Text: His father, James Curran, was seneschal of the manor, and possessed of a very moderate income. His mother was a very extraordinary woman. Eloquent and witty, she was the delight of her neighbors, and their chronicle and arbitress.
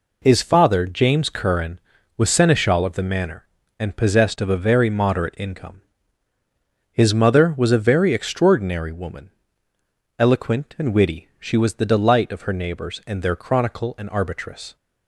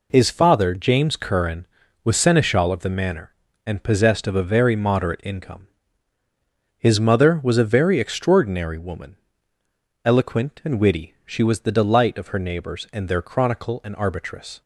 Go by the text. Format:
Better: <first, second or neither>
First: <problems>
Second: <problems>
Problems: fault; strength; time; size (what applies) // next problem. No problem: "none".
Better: neither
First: none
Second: none